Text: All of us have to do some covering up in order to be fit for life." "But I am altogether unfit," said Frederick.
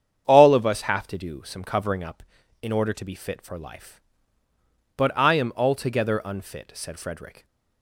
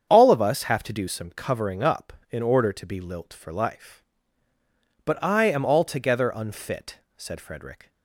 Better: first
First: starts louder than the rest; strong; until 1.2 s; 8 dB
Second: starts louder than the rest; strong; until 1.1 s; 7.5 dB // says "lilt" for "fit"; at 2.9 s

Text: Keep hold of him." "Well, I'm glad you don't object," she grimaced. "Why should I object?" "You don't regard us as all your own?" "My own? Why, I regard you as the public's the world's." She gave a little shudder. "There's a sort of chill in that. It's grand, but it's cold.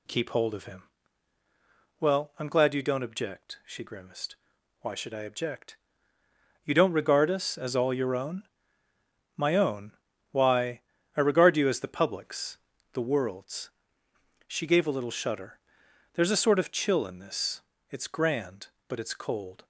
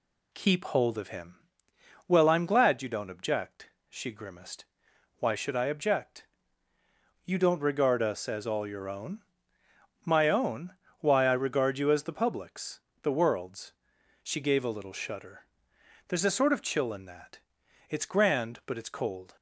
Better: second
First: pauses between "public's" and "the"; slight; at 12.5 s; 0.36 s long // says "this" for "that"; at 17.1 s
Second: pauses between "public's" and "the"; slight; at 12.7 s; 0.22 s long

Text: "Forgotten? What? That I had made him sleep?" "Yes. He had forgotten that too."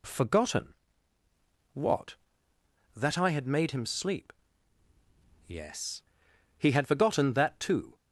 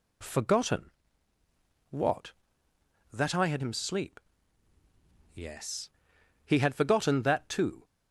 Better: first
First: none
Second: skips "made"; at 3.6 s

